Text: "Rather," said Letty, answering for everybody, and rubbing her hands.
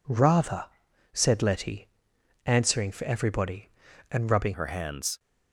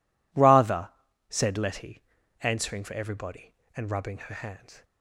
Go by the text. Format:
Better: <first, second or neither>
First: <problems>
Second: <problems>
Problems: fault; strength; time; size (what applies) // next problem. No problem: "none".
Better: second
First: changes voice at "her"; from 4.5 s on; 0.6 s long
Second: none